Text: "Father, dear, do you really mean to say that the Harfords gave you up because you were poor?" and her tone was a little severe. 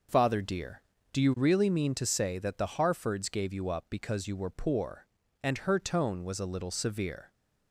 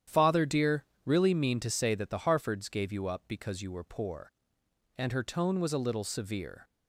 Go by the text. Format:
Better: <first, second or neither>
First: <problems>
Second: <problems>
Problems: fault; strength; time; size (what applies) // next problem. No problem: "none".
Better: first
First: none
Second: starts louder than the rest; strong; until 1.2 s; 10 dB // skips "do you"; at 0.9 s